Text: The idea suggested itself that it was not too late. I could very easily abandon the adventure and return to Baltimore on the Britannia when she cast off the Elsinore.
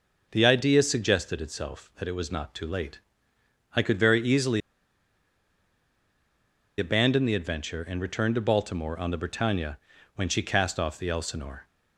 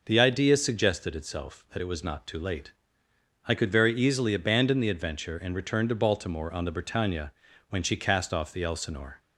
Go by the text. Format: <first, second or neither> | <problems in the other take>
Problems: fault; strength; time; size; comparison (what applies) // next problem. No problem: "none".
second | pauses between "easily" and "abandon"; strong; at 4.6 s; 2.1 s long // pauses between "Britannia" and "when"; slight; at 9.7 s; 0.36 s long; slight in the second